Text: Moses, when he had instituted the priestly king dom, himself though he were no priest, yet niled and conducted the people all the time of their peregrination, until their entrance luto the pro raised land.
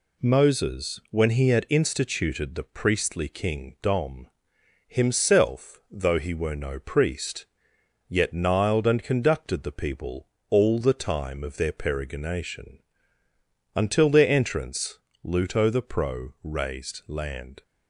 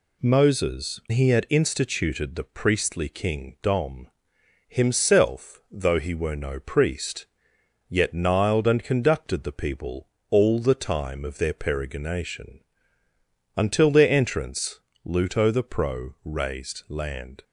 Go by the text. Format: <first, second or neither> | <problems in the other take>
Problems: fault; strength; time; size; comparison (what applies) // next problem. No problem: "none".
first | skips "when"; at 1.0 s // pauses between "people" and "all"; slight; at 10.0 s; 0.22 s long; slight in the first // pauses between "entrance" and "luto"; slight; at 14.7 s; 0.26 s long; slight in the first